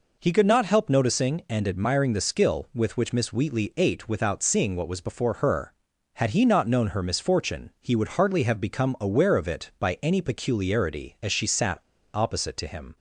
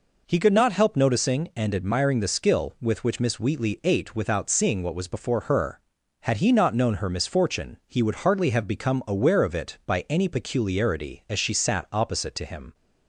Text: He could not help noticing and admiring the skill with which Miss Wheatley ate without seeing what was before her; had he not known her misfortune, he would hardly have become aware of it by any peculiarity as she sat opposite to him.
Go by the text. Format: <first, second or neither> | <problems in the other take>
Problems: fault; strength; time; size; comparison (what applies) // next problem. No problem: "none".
second | pauses between "sat" and "opposite"; slight; at 11.7 s; 0.36 s long